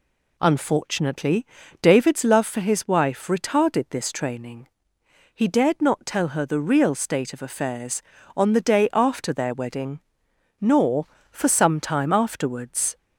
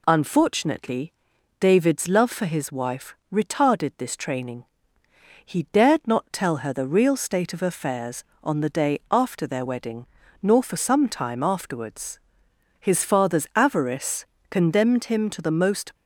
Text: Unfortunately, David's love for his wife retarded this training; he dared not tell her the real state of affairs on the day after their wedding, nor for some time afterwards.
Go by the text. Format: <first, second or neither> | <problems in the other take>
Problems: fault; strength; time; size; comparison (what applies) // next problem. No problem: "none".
first | pauses between "wife" and "retarded"; slight; at 3.1 s; 0.18 s long // goes on to say "His father's avarice condemned him to the most"; strong; from 12.8 s on; 3.1 s long